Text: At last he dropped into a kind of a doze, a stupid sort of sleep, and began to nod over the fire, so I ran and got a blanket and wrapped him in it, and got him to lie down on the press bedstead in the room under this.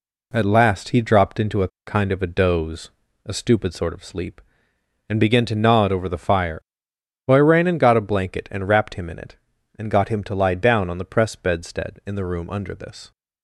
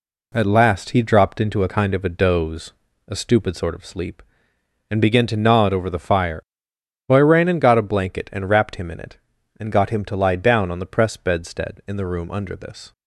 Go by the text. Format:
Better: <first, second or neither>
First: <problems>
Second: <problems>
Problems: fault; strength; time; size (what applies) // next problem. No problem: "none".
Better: second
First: pauses between "a" and "kind"; slight; at 1.6 s; 0.18 s long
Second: none